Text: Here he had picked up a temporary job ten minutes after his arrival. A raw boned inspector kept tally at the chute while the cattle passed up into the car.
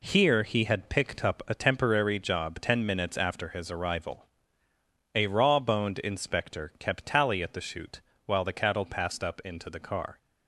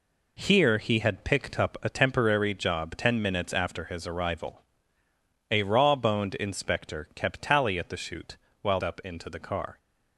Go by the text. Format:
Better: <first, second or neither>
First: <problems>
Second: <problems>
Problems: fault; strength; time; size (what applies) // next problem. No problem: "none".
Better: first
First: pauses between "chute" and "while"; slight; at 8.0 s; 0.24 s long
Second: pauses between "chute" and "while"; slight; at 8.3 s; 0.24 s long // skips "the cattle passed"; at 8.8 s